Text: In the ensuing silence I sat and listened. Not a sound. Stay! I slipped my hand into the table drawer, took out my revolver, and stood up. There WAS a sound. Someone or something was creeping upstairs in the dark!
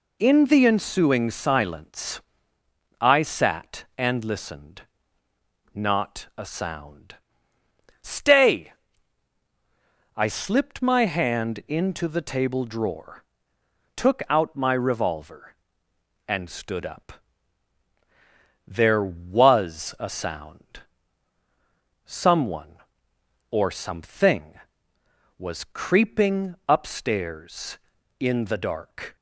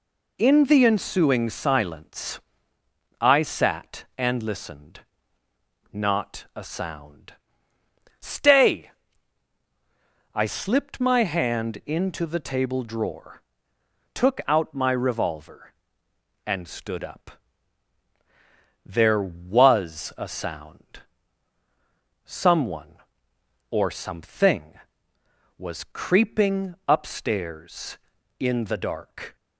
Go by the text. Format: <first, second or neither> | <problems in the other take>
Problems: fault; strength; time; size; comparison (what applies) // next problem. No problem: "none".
neither | pauses between "silence" and "I"; noticeable; the same in both